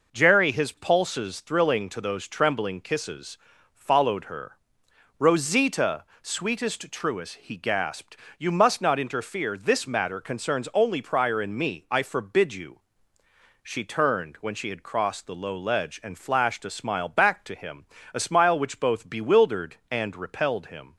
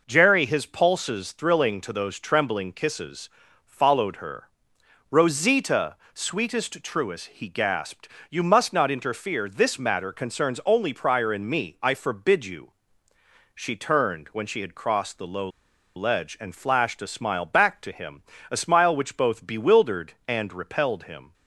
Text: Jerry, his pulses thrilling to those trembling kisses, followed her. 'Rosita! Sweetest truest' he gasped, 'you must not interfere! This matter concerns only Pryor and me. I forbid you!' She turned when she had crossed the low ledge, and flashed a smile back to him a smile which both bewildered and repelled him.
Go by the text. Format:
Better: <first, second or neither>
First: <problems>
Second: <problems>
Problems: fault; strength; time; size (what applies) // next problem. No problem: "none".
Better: first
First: pauses between "him" and "a"; slight; at 17.8 s; 0.26 s long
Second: pauses between "low" and "ledge"; noticeable; at 15.4 s; 0.48 s long // pauses between "him" and "a"; slight; at 18.2 s; 0.26 s long